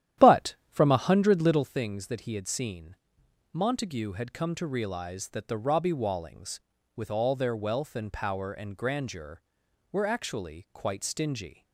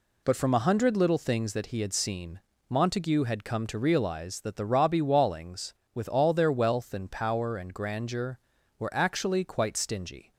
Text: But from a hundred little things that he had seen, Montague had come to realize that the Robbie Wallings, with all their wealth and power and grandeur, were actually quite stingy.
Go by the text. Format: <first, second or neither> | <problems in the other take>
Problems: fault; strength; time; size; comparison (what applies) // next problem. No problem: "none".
second | starts louder than the rest; strong; until 1.7 s; 11.5 dB